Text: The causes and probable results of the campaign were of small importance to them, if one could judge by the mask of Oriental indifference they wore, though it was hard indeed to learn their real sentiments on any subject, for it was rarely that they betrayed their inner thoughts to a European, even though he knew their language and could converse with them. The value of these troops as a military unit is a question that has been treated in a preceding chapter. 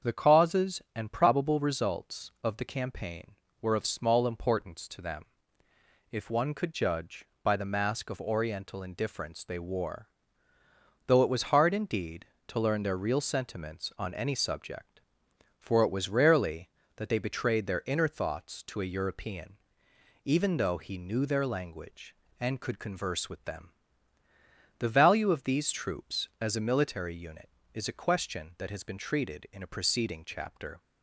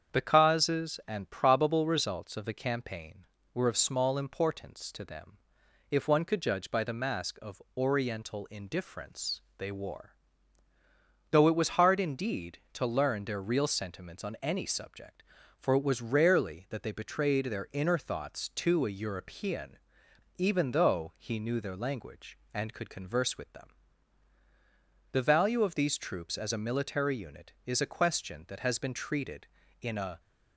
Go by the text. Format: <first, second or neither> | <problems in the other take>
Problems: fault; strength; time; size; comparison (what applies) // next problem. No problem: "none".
first | starts louder than the rest; strong; until 1.2 s; 7.5 dB; also in the first // pauses between "of" and "Oriental"; slight; at 7.6 s; 0.16 s long // pauses between "indifference" and "they"; slight; at 9.4 s; 0.16 s long // stops before "preceding chapter"; at 30.1 s